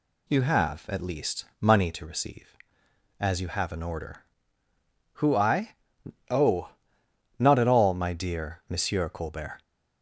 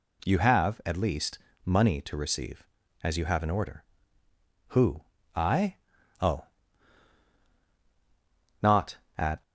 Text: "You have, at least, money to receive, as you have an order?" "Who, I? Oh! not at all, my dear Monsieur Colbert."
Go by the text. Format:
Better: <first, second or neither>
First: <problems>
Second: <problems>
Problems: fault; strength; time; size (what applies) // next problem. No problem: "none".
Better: first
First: none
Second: stops before "all my dear Monsieur Colbert"; at 9.4 s